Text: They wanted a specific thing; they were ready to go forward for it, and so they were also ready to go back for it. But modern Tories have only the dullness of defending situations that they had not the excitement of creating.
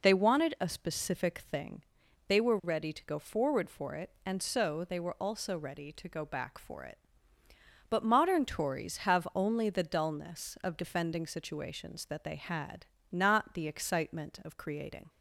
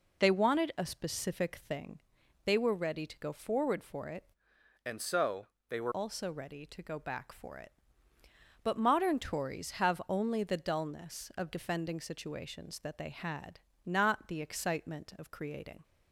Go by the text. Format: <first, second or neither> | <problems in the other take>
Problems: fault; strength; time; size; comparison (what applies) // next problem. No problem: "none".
first | changes voice from "and" to "were"; from 4.8 to 5.9 s; 1.1 s long // pauses between "so" and "they"; slight; at 5.4 s; 0.20 s long // pauses between "had" and "not"; slight; at 13.5 s; 0.26 s long; slight in the first